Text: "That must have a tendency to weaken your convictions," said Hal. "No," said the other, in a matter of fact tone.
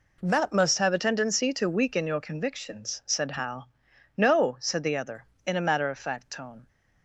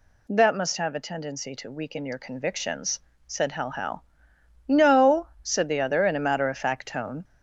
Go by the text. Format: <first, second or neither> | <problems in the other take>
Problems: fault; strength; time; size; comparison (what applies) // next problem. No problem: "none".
first | says "Hal" twice; at 3.6 s